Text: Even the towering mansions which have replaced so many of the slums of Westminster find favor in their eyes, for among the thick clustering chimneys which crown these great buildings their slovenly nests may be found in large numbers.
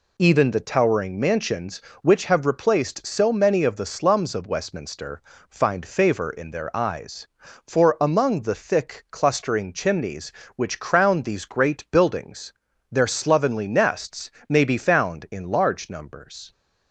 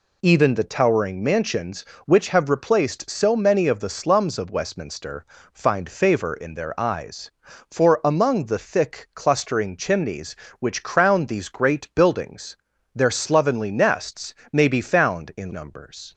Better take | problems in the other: first | pauses between "Westminster" and "find"; slight; at 5.2 s; 0.26 s long; slight in the first // pauses between "buildings" and "their"; at 12.5 s; 0.38 s long; also in the first // pauses between "nests" and "may"; slight; at 14.3 s; 0.20 s long; slight in the first // skips "large"; at 15.5 s

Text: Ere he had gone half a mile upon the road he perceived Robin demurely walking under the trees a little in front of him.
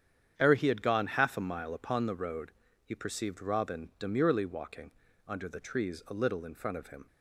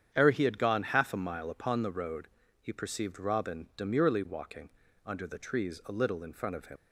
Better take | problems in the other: first | starts louder than the rest; strong; until 1.1 s; 8.5 dB; strong in the first // pauses between "road" and "he"; slight; at 2.2 s; 0.32 s long; slight in the first // pauses between "walking" and "under"; at 4.6 s; 0.38 s long; also in the first // leaves "him" unfinished; at 6.7 s; 90 ms

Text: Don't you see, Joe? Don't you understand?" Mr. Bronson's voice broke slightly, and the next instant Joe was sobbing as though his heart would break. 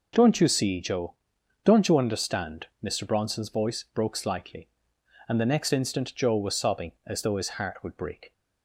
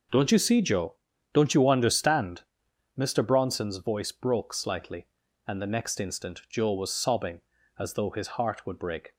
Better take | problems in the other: neither | none

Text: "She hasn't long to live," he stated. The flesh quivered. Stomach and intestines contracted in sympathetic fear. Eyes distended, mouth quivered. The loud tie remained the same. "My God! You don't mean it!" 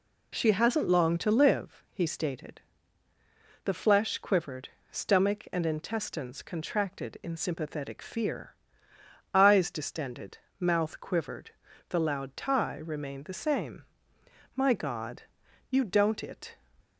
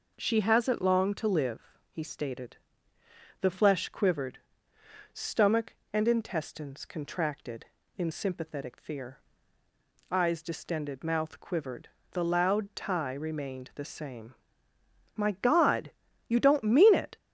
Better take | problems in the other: second | skips "mean"; at 16.2 s

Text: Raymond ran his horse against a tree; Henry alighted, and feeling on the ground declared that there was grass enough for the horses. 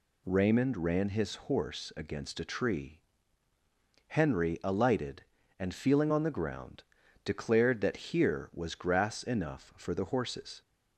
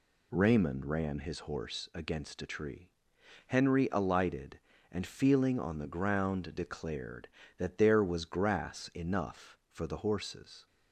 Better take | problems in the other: second | pauses between "ground" and "declared"; at 6.8 s; 0.42 s long // says "here" for "there"; at 8.1 s

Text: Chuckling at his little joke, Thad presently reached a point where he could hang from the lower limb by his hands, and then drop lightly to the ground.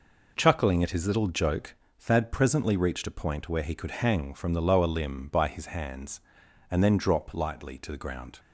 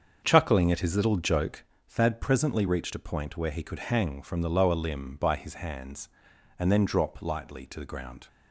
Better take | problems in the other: first | starts louder than the rest; until 1.6 s; 7 dB

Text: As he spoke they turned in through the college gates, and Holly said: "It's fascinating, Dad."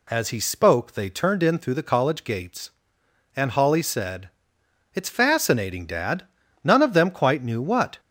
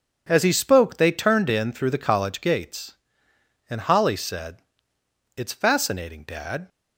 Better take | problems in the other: second | goes on to say "None of them quite knew what"; from 6.6 s on; 1.3 s long

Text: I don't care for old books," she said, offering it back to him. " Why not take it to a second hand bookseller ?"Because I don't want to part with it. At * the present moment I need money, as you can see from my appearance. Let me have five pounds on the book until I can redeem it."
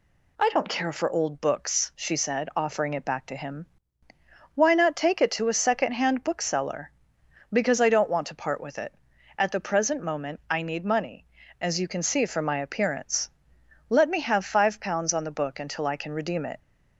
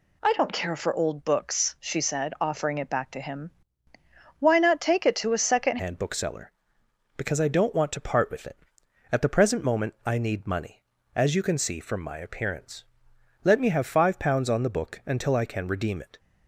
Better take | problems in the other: first | changes voice at "hand"; from 5.7 s on; 10.4 s long

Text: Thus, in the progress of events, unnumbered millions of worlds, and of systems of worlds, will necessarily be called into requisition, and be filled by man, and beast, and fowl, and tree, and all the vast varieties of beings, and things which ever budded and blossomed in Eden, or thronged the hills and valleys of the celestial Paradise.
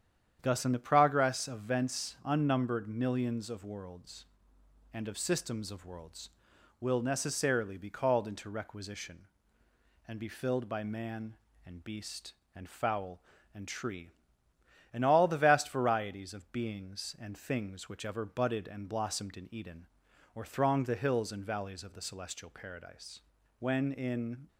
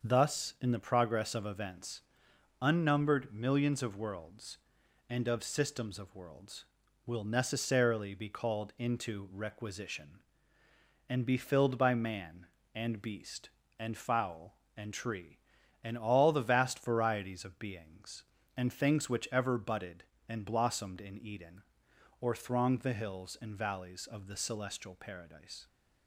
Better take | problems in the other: second | starts louder than the rest; strong; until 1.4 s; 9 dB; also in the second // goes on to say "When in"; noticeable; from 23.5 s on; 0.88 s long

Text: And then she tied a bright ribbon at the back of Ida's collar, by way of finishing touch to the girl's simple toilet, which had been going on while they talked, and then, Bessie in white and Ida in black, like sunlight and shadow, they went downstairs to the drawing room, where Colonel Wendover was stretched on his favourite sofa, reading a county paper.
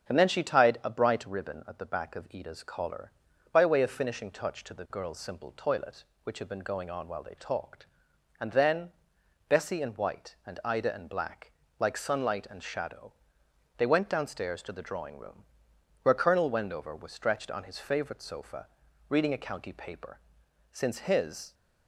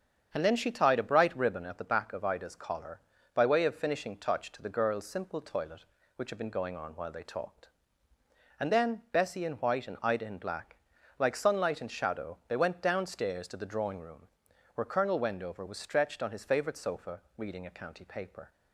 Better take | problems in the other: second | starts louder than the rest; strong; until 1.1 s; 8 dB; strong in the second // goes on to say "Since his"; noticeable; from 20.7 s on; 0.82 s long

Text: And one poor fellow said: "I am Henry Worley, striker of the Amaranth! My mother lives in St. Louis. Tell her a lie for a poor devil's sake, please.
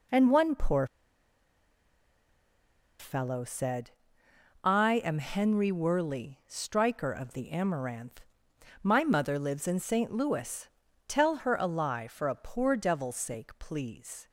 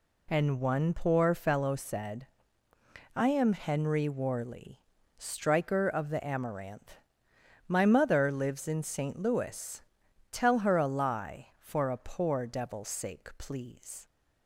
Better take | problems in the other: second | pauses between "poor" and "fellow"; strong; at 0.8 s; 2.1 s long

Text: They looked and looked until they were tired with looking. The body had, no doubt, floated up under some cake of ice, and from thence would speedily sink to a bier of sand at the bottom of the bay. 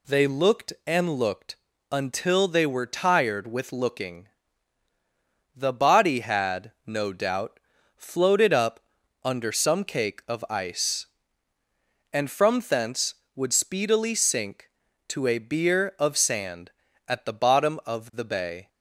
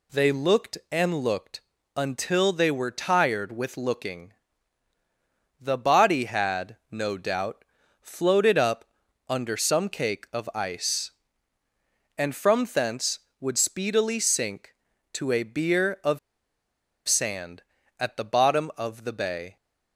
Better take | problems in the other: first | pauses between "looked" and "until"; slight; at 1.5 s; 0.36 s long; slight in the first // pauses between "up" and "under"; at 8.8 s; 0.42 s long; also in the first // pauses between "of" and "sand"; noticeable; at 16.1 s; 0.89 s long

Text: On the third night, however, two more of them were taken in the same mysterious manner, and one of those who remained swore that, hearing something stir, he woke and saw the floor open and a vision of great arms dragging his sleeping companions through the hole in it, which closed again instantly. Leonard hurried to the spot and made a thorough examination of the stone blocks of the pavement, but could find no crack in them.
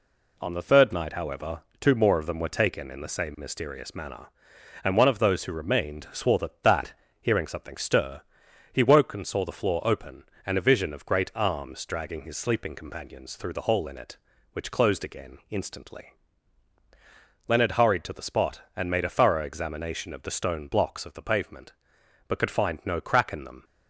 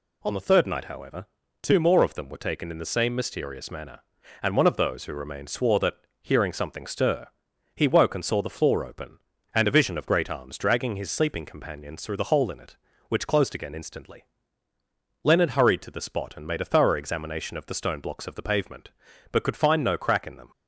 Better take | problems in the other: second | says "that" twice; at 6.6 s

